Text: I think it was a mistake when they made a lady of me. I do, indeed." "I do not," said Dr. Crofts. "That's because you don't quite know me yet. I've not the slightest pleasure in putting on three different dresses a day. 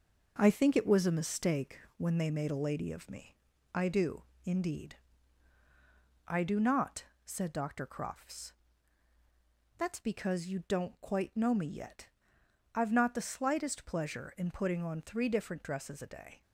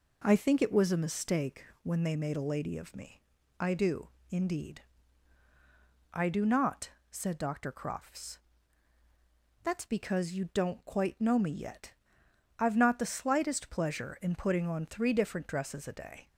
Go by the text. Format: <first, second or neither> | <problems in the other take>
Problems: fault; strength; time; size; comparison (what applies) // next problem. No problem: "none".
second | gets quieter; noticeable; throughout; 5.5 dB // pauses between "mistake" and "when"; slight; at 1.7 s; 0.18 s long; slight in the second